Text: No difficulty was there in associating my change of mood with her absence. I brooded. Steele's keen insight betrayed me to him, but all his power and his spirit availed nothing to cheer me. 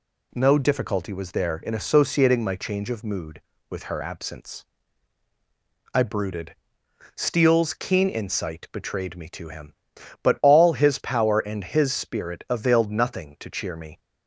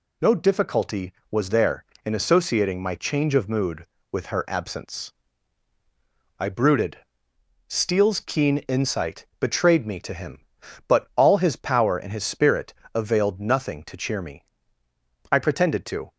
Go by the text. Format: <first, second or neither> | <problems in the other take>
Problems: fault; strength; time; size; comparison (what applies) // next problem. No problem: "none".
first | pauses between "spirit" and "availed"; slight; at 12.7 s; 0.22 s long // goes on to say "I pretended to"; noticeable; from 15.3 s on; 0.80 s long